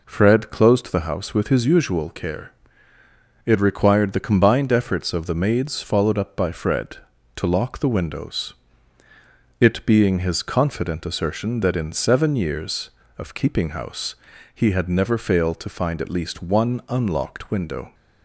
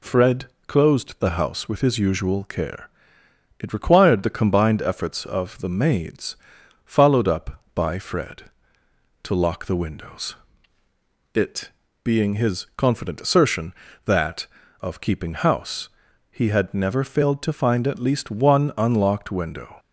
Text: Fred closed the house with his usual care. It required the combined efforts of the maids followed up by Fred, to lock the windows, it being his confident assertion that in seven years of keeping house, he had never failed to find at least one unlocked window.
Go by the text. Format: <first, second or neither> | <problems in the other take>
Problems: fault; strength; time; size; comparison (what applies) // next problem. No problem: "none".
first | pauses between "Fred" and "closed"; slight; at 0.4 s; 0.22 s long // pauses between "maids" and "followed"; noticeable; at 6.3 s; 0.50 s long // pauses between "it" and "being"; slight; at 11.7 s; 0.32 s long // skips "in seven years"; at 14.6 s